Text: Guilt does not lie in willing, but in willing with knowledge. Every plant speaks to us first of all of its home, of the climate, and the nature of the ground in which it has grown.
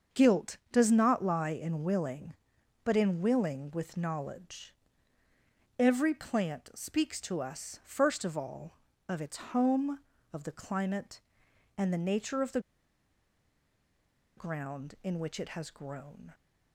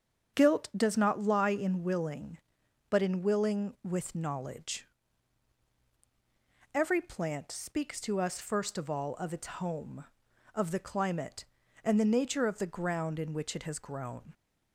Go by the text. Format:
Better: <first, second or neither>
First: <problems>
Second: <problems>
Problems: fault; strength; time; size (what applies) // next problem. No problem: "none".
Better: second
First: starts louder than the rest; until 1.2 s; 7 dB // pauses between "the" and "ground"; strong; at 12.5 s; 1.7 s long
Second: starts louder than the rest; strong; until 1.4 s; 8 dB